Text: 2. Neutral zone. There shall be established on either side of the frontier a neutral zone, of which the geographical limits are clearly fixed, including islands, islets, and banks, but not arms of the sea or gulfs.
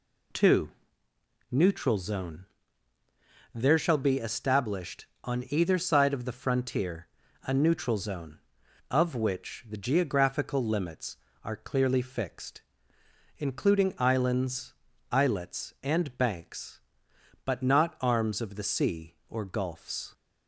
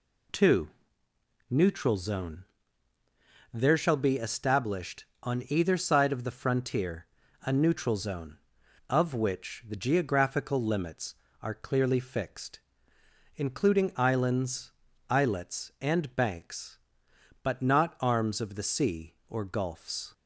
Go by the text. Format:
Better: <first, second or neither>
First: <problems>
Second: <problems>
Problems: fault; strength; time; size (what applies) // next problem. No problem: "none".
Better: neither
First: pauses between "frontier" and "a"; slight; at 7.0 s; 0.36 s long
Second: pauses between "frontier" and "a"; slight; at 7.0 s; 0.36 s long